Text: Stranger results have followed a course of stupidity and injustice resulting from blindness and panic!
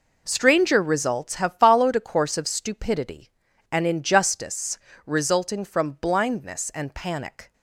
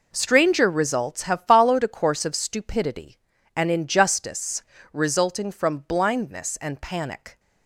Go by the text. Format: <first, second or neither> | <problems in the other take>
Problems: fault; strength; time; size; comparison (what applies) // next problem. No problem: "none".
neither | pauses between "injustice" and "resulting"; slight; the same in both